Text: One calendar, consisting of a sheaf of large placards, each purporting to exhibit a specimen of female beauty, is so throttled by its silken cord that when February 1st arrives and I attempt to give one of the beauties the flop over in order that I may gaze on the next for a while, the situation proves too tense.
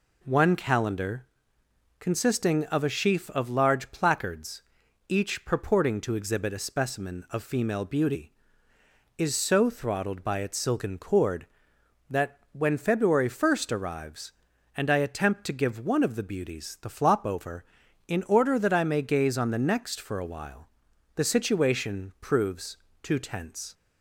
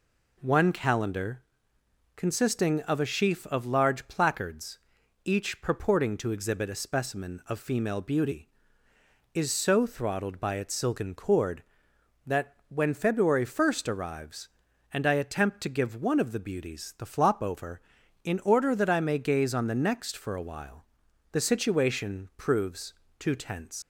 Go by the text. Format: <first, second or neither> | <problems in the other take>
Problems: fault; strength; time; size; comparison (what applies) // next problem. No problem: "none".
first | pauses between "that" and "when"; slight; at 12.5 s; 0.16 s long; slight in the first // pauses between "proves" and "too"; slight; at 22.9 s; 0.24 s long; slight in the first // leaves "tense" unfinished; at 23.8 s; 75 ms